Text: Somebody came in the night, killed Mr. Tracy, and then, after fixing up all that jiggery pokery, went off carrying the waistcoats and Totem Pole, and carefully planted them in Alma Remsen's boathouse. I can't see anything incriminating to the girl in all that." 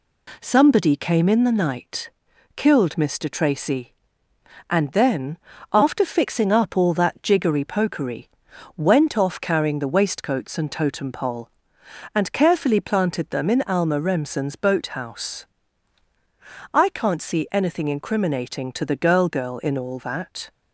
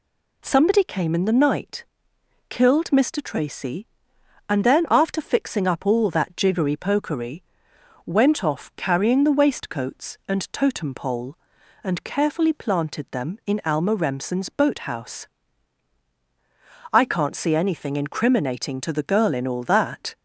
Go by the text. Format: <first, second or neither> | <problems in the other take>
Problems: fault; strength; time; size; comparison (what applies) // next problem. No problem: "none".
second | says "girl" twice; at 19.2 s